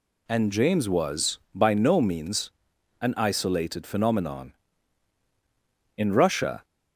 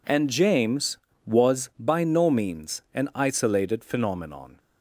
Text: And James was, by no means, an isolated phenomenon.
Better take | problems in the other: second | goes on to say "In Russia"; noticeable; from 5.9 s on; 0.66 s long

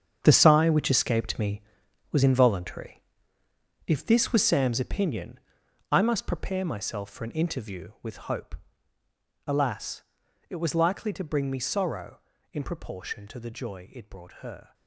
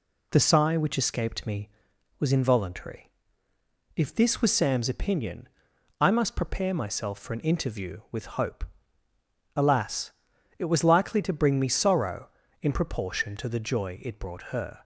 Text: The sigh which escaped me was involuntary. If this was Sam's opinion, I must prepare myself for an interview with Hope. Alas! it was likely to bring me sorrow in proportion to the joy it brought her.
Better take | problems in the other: second | gets quieter; strong; throughout; 11.5 dB

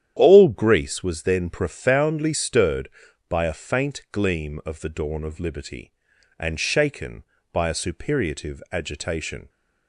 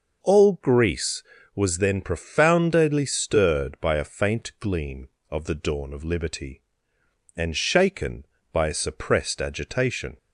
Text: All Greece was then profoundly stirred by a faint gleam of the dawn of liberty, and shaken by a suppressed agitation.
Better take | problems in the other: second | starts louder than the rest; strong; until 1.1 s; 10 dB // says "superiative" for "suppressed"; at 7.7 s

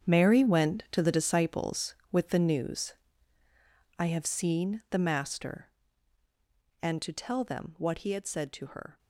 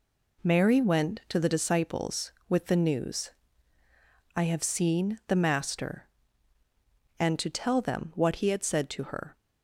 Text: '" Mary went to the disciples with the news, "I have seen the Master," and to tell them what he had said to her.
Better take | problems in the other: second | gets quieter; strong; throughout; 13.5 dB

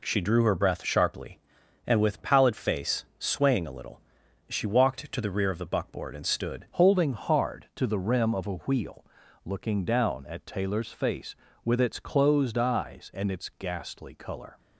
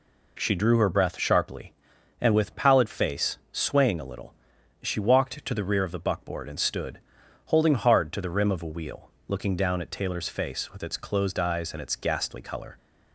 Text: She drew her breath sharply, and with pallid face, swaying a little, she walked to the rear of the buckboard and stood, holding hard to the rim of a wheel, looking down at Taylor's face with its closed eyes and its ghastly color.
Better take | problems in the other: second | changes voice at "holding"; from 6.7 s on; 7.8 s long

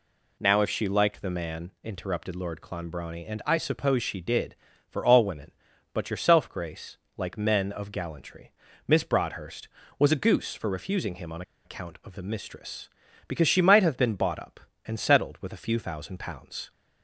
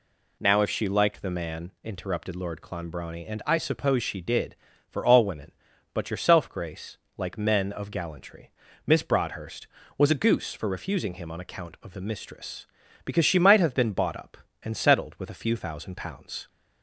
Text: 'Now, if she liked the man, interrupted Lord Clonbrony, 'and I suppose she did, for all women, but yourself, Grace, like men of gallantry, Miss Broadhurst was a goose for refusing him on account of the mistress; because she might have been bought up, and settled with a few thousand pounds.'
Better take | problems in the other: second | pauses between "on" and "account"; slight; at 11.4 s; 0.23 s long

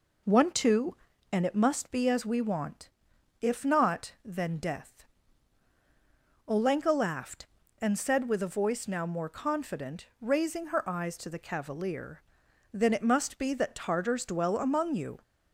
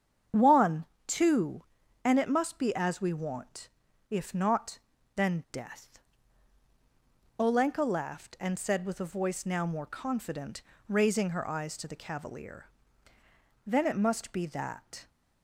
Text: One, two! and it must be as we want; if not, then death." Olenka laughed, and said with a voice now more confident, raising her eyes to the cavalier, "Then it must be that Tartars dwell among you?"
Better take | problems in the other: first | starts louder than the rest; strong; until 1.5 s; 8 dB // stops before "Tartars dwell among you"; at 15.0 s

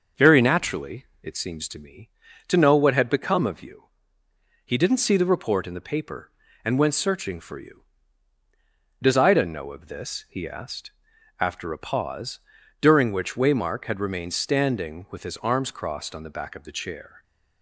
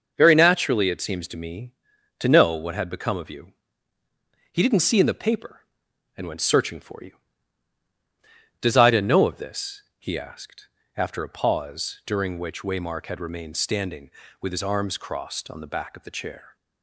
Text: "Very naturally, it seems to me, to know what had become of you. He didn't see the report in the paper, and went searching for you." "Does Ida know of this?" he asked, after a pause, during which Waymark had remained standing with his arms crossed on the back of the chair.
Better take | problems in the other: first | starts louder than the rest; noticeable; until 1.1 s; 6 dB; noticeable in the first // skips "the report"; at 4.9 s

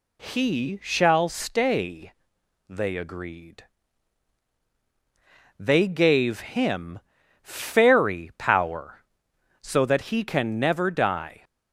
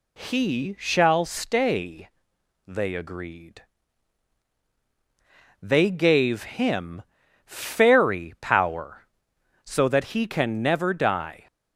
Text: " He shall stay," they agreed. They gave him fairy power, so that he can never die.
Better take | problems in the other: neither | pauses between "him" and "fairy"; noticeable; the same in both

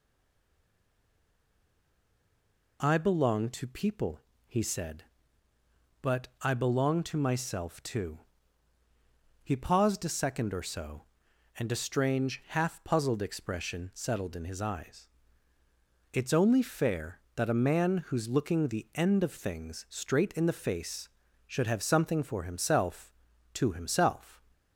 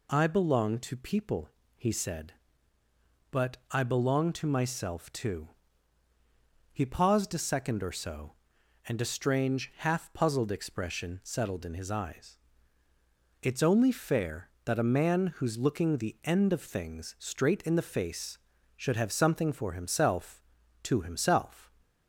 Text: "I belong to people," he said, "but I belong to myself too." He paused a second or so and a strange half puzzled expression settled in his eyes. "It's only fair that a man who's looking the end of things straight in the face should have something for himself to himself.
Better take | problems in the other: second | stays silent before the first word; strong; until 2.7 s; 2.7 s long

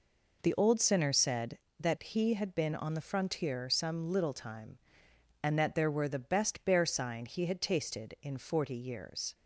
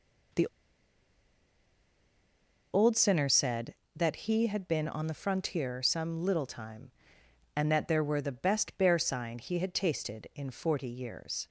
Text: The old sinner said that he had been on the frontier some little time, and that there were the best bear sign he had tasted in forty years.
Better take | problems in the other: first | pauses between "The" and "old"; strong; at 0.4 s; 2.2 s long

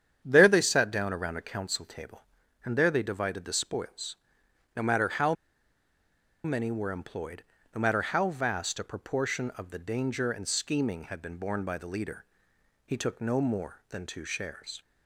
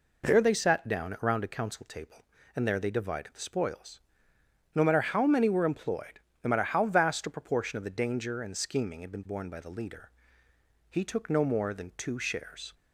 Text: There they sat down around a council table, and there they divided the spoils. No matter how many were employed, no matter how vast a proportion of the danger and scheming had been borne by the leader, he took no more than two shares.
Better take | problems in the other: second | starts louder than the rest; strong; until 1.2 s; 8.5 dB // pauses between "how" and "many"; at 5.3 s; 1.1 s long

